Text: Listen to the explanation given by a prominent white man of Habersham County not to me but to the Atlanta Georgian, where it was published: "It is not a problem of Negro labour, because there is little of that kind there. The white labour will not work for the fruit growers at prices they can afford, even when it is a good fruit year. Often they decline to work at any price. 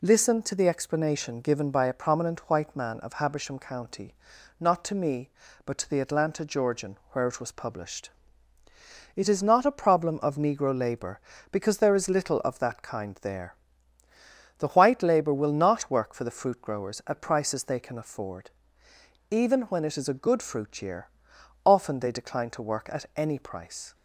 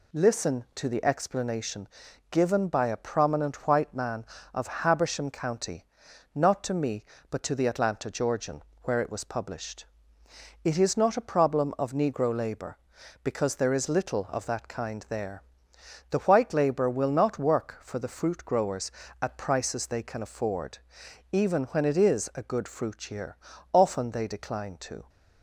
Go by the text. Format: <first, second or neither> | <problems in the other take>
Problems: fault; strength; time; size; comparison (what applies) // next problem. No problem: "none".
first | pauses between "explanation" and "given"; at 1.8 s; 0.44 s long // pauses between "County" and "not"; noticeable; at 5.8 s; 0.50 s long; noticeable in the first // stops before "work at any price"; at 25.0 s